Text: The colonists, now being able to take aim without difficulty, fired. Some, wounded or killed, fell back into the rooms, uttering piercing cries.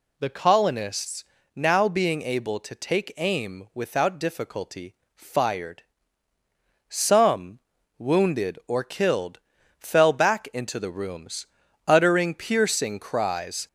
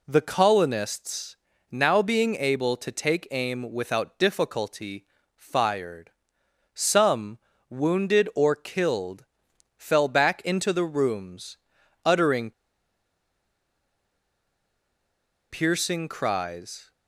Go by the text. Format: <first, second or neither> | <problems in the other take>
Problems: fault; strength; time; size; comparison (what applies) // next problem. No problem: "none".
first | pauses between "uttering" and "piercing"; strong; at 12.5 s; 2.9 s long